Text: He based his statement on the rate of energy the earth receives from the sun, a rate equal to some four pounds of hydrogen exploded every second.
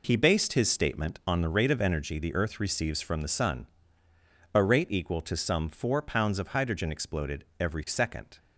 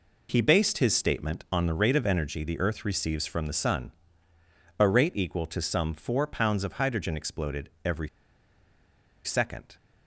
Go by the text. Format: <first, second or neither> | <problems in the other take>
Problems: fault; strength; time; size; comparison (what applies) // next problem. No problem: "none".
first | pauses between "exploded" and "every"; slight; at 7.6 s; 0.16 s long; slight in the first // pauses between "every" and "second"; at 8.0 s; 1.1 s long